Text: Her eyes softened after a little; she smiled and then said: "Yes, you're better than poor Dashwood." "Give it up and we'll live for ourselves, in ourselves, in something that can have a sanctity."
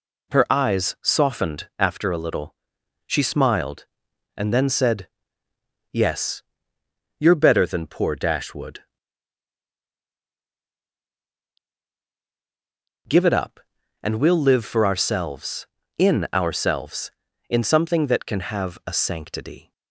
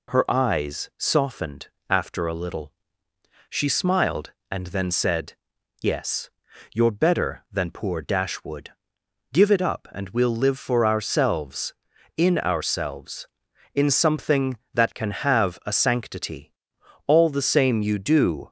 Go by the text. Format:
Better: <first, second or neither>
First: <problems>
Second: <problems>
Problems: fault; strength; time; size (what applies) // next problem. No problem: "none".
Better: first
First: none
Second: pauses between "softened" and "after"; slight; at 1.6 s; 0.20 s long // goes on to say "All the same you do"; from 17.0 s on; 1.4 s long